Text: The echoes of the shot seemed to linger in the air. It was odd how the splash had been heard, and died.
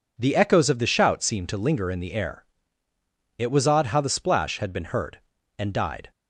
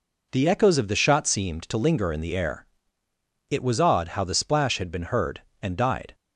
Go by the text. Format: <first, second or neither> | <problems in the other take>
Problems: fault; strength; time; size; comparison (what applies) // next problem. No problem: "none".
second | says "shout" for "shot"; at 0.8 s